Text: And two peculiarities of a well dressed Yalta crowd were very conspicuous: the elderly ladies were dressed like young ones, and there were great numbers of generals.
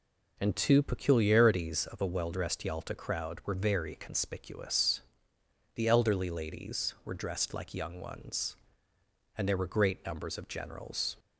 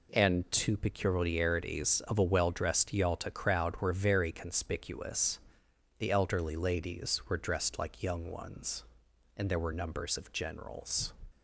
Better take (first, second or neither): first